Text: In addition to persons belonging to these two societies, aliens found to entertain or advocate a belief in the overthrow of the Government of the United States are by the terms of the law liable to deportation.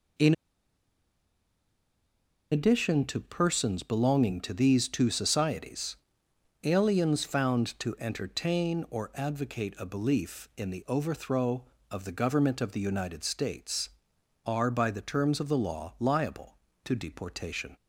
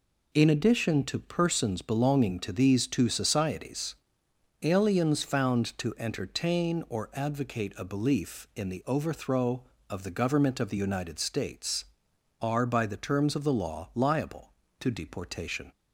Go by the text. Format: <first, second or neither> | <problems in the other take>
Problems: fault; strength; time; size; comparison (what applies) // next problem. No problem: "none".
second | pauses between "In" and "addition"; strong; at 0.3 s; 2.1 s long